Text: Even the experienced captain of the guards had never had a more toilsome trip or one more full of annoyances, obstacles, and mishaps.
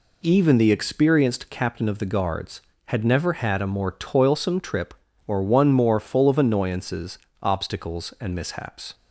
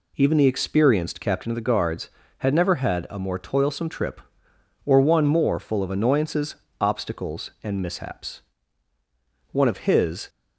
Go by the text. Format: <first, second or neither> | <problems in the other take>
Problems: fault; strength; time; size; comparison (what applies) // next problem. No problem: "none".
first | goes on to say "One of his"; noticeable; from 9.5 s on; 0.78 s long